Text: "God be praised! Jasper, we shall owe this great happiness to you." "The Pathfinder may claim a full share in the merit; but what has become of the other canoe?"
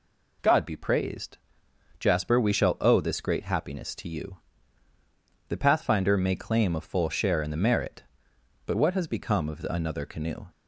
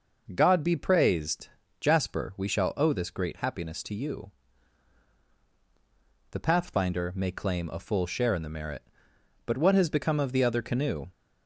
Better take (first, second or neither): second